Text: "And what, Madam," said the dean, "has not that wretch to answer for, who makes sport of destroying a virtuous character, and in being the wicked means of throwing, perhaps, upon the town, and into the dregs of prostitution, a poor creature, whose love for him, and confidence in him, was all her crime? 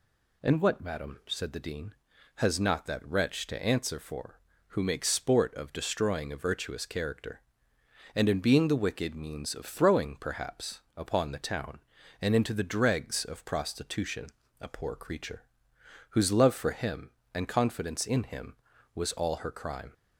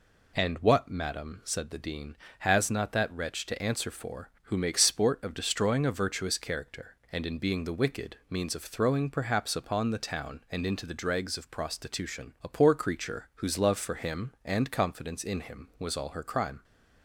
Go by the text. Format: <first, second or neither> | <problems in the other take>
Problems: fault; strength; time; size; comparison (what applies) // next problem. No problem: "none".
neither | none